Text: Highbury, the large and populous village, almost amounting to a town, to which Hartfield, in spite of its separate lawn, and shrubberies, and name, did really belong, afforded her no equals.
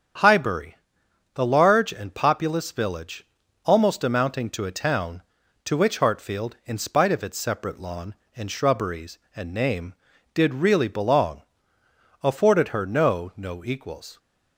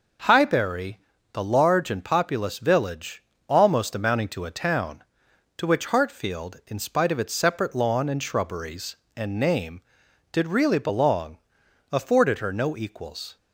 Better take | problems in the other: second | starts louder than the rest; strong; until 1.7 s; 8 dB // says "no" twice; at 13.3 s

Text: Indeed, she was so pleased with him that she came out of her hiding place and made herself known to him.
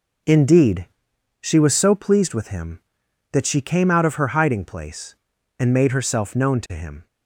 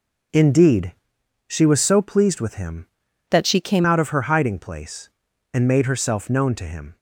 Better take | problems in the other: first | changes voice from "that" to "came"; from 3.2 to 3.8 s; 0.6 s long

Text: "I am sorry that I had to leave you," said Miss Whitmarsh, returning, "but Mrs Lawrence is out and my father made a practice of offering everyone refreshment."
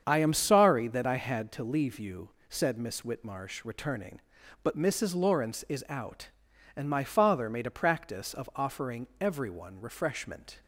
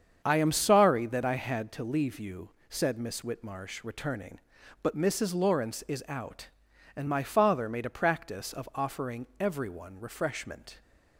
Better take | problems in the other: neither | starts louder than the rest; strong; the same in both

